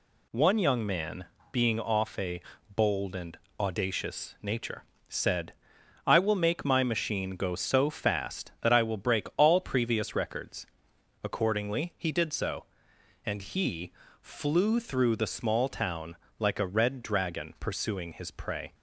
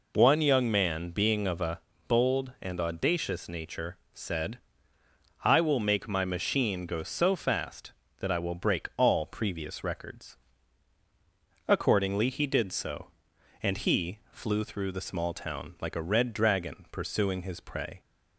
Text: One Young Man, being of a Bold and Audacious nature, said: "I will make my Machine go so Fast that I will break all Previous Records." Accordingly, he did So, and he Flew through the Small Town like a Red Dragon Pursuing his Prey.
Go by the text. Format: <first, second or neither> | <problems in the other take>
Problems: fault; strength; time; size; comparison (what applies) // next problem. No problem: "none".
second | says "off" for "of"; at 1.8 s // pauses between "a" and "Bold"; slight; at 2.4 s; 0.34 s long; slight in the second // pauses between "and" and "Audacious"; slight; at 3.3 s; 0.20 s long // pauses between "he" and "Flew"; slight; at 13.9 s; 0.30 s long // pauses between "Town" and "like"; slight; at 16.1 s; 0.24 s long